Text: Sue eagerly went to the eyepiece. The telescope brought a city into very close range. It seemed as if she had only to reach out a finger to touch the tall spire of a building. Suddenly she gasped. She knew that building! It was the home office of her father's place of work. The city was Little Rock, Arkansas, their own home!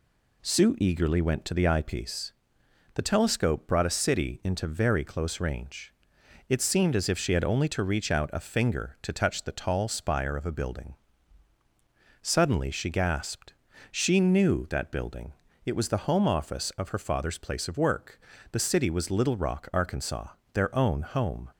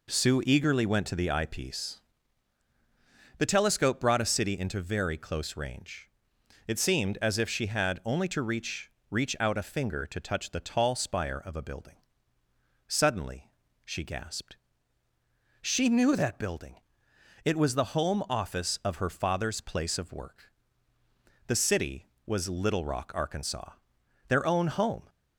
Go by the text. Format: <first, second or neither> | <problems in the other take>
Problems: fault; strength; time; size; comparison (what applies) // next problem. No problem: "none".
first | says "reach" twice; at 9.1 s // pauses between "Suddenly" and "she"; slight; at 13.5 s; 0.34 s long